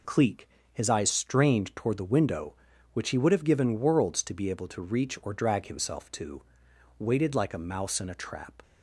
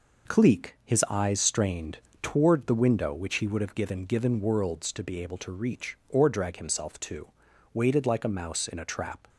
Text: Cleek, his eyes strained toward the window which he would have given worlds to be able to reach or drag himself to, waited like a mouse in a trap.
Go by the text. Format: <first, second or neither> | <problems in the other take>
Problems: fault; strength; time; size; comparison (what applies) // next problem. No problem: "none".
first | pauses between "strained" and "toward"; slight; at 1.9 s; 0.22 s long // says "given" twice; at 4.0 s